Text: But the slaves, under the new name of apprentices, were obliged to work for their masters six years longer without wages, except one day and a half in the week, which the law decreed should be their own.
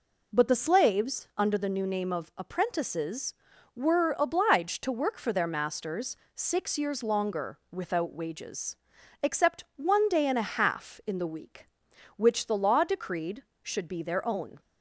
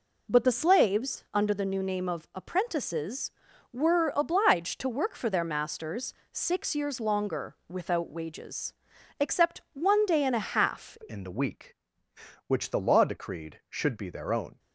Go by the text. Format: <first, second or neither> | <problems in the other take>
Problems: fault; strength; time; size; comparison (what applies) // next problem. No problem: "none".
first | pauses between "masters" and "six"; slight; at 6.1 s; 0.18 s long; slight in the first // changes voice at "in"; from 11.0 s on; 3.5 s long